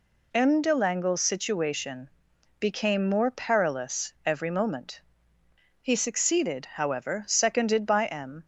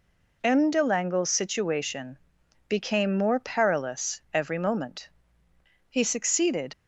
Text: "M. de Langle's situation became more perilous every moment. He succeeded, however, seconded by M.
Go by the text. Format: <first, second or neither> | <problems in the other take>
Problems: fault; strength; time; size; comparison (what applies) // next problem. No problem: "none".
first | pauses between "situation" and "became"; noticeable; at 2.1 s; 0.52 s long; noticeable in the first // stops before "however seconded by M"; at 6.7 s